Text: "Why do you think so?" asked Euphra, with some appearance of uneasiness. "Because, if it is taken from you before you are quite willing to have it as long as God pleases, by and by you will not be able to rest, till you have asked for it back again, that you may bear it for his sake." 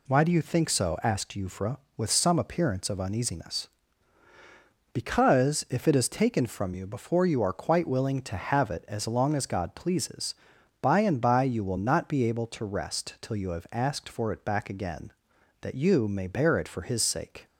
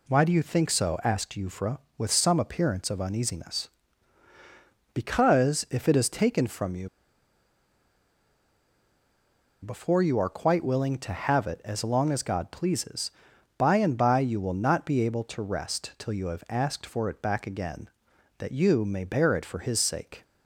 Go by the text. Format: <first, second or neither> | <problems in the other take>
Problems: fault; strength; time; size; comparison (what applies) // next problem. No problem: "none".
first | pauses between "you" and "before"; strong; at 6.8 s; 2.7 s long